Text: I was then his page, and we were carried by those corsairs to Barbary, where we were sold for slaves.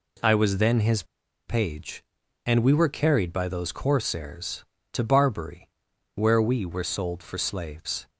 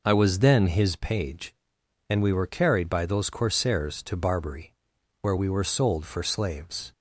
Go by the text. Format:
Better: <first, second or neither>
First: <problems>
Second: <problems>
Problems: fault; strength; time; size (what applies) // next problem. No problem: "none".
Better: second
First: pauses between "his" and "page"; at 1.0 s; 0.43 s long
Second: none